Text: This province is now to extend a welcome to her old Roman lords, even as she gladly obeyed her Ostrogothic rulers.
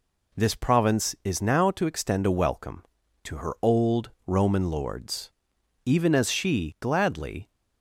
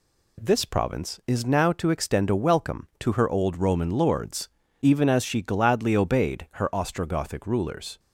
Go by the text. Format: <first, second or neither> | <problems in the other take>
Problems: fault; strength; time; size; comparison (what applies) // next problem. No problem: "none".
second | pauses between "old" and "Roman"; slight; at 4.0 s; 0.18 s long // stops before "obeyed her Ostrogothic rulers"; at 7.5 s